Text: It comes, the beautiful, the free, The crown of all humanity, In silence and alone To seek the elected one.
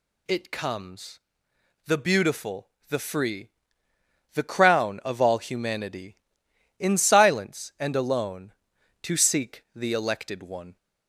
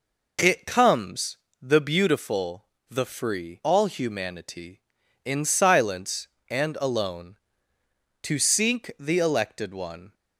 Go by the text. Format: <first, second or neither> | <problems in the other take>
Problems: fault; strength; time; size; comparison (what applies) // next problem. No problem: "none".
first | skips "The crown of"; at 3.6 s